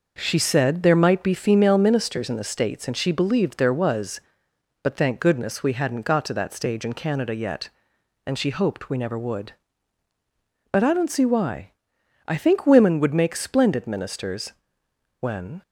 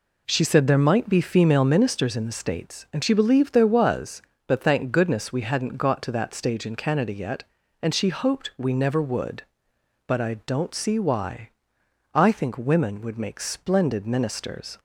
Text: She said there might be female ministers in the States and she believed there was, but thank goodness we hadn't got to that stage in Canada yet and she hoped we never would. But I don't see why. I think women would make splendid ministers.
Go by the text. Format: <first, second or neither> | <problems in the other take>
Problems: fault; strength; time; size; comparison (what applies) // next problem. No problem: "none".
second | goes on to say "When"; slight; from 15.1 s on; 0.42 s long